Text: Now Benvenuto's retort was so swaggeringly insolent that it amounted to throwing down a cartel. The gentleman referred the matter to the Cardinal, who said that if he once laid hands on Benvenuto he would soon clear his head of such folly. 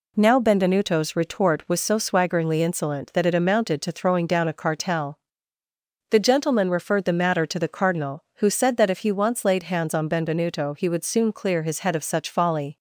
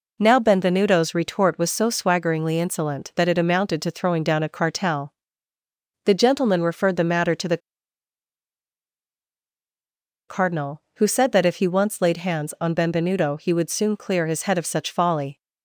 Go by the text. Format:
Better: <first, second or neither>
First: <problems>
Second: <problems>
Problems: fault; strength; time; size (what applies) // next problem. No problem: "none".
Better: first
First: none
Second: pauses between "the" and "Cardinal"; strong; at 7.5 s; 2.7 s long